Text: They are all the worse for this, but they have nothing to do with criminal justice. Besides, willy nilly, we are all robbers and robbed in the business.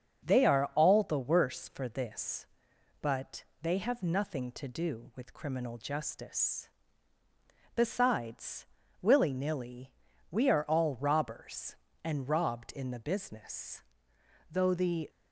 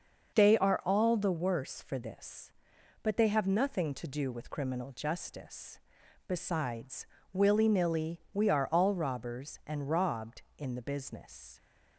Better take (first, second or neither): second